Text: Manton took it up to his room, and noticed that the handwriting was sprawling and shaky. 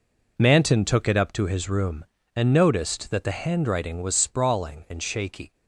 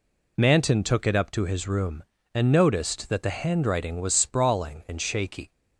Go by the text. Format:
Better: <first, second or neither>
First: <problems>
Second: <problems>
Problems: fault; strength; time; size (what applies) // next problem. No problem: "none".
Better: second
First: gets quieter; strong; throughout; 12 dB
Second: none